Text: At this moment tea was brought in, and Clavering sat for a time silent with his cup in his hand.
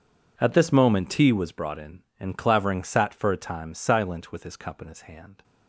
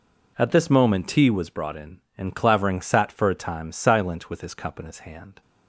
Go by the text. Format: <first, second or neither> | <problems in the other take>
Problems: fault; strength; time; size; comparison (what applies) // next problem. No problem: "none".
second | gets quieter; strong; throughout; 18.5 dB